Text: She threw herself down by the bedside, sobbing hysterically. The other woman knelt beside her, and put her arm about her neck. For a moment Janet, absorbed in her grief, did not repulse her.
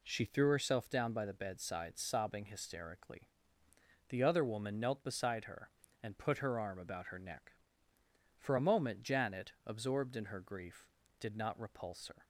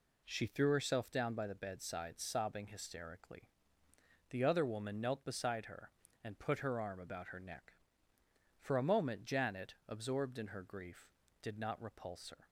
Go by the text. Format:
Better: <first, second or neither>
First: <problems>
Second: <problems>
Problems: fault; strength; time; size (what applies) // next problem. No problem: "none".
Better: neither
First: none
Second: none